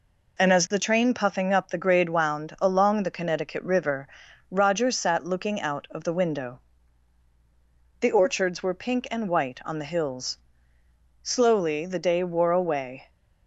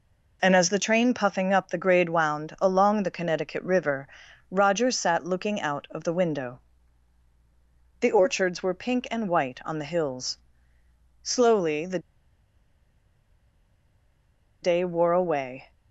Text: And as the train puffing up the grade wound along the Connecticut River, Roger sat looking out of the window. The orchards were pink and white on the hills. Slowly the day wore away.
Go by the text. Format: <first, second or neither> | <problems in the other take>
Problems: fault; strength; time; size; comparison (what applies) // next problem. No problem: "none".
first | pauses between "the" and "day"; strong; at 11.9 s; 2.6 s long